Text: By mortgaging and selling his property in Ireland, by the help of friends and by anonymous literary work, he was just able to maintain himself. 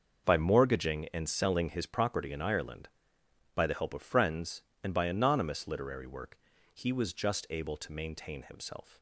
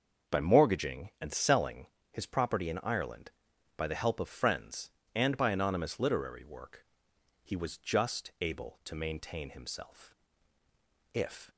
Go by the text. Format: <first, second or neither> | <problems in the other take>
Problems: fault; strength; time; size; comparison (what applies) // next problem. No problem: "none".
first | starts louder than the rest; until 1.4 s; 6.5 dB; also in the first // pauses between "selling" and "his"; slight; at 1.8 s; 0.26 s long // goes on to say "If"; slight; from 11.1 s on; 0.36 s long